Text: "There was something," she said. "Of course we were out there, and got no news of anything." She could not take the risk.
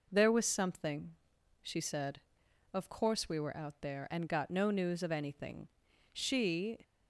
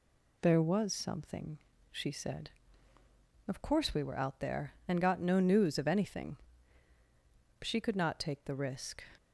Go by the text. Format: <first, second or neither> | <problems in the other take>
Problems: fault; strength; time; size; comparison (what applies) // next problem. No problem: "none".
second | stops before "could not take the risk"; at 6.8 s